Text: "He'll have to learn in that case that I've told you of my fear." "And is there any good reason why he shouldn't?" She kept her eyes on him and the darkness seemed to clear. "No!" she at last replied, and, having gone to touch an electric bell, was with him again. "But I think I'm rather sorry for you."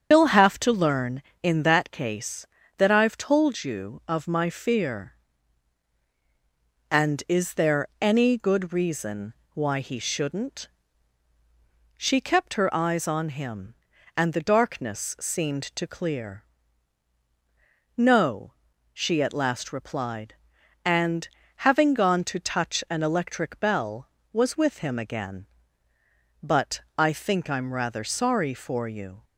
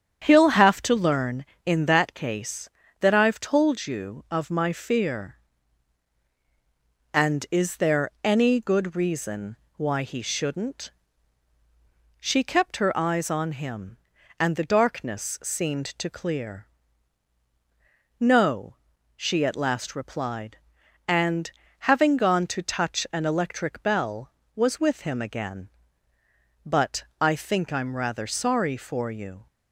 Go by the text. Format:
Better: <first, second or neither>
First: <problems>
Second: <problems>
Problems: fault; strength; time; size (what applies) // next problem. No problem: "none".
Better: second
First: loses the start of "He'll"; at 0.1 s; 120 ms // starts louder than the rest; strong; until 1.1 s; 8 dB // pauses between "reason" and "why"; slight; at 9.3 s; 0.18 s long // pauses between "But" and "I"; slight; at 26.7 s; 0.18 s long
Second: starts louder than the rest; strong; until 1.2 s; 8.5 dB // pauses between "reason" and "why"; slight; at 9.5 s; 0.18 s long // pauses between "But" and "I"; slight; at 27.0 s; 0.18 s long